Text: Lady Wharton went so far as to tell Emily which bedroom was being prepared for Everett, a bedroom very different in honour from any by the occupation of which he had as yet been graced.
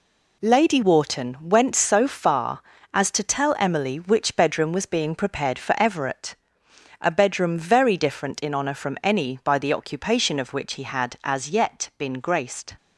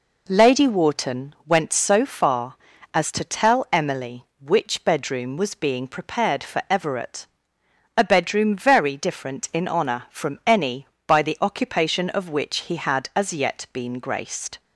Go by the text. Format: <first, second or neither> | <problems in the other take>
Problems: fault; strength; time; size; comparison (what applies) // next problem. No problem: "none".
neither | none